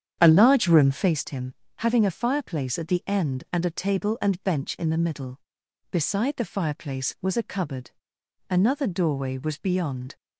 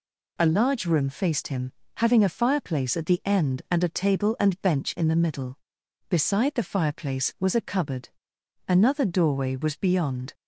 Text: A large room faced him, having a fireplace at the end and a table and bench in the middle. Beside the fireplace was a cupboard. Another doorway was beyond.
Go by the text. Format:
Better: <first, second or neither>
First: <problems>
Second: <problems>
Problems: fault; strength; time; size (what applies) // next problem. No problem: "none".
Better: second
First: starts louder than the rest; strong; until 1.2 s; 8.5 dB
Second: none